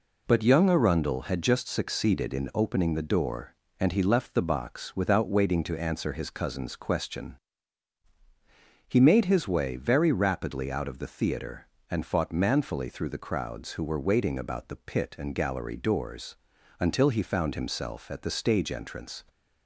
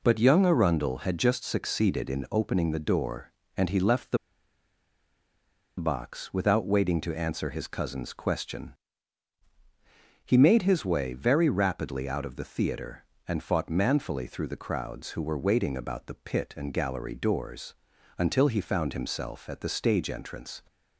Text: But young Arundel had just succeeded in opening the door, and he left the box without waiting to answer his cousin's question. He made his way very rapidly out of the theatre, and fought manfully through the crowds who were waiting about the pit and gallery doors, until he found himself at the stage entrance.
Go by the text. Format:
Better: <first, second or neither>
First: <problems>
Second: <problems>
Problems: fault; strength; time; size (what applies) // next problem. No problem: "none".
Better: first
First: none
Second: pauses between "the" and "box"; strong; at 4.1 s; 1.6 s long